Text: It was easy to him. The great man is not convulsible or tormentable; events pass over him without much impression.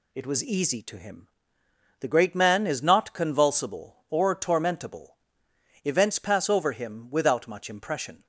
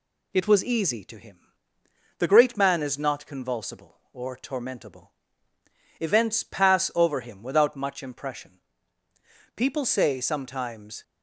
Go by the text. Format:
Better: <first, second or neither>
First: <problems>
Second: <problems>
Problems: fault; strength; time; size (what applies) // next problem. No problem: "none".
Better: first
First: none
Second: goes on to say "People say sometimes"; from 9.5 s on; 1.4 s long